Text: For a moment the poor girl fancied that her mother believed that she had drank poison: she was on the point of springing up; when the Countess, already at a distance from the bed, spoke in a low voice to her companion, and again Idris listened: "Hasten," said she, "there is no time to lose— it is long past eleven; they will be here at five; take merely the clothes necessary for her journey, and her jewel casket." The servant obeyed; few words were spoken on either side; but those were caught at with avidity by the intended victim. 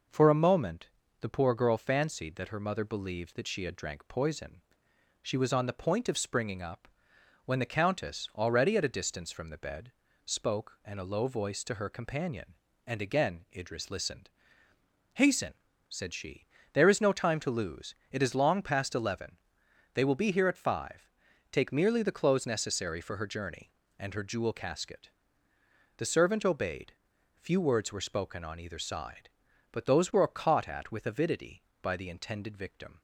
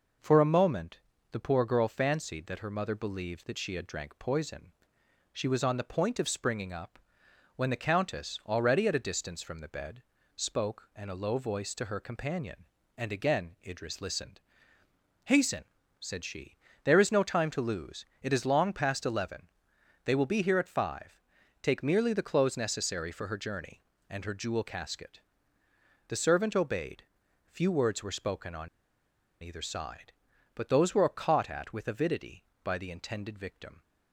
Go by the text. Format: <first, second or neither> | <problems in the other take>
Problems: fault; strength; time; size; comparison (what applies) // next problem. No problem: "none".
first | pauses between "moment" and "the"; slight; at 0.9 s; 0.32 s long; slight in the first // pauses between "on" and "either"; noticeable; at 28.6 s; 0.74 s long